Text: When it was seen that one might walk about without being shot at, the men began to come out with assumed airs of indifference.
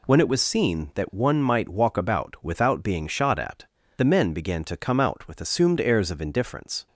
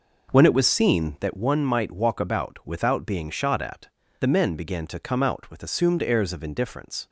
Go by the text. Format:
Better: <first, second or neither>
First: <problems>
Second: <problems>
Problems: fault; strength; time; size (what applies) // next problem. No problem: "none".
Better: first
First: none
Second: starts louder than the rest; noticeable; until 1.4 s; 5 dB